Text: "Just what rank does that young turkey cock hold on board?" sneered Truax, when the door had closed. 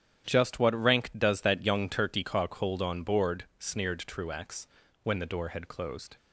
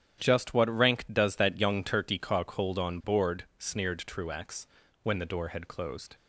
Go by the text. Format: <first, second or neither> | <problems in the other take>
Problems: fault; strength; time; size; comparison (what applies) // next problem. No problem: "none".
neither | starts louder than the rest; strong; the same in both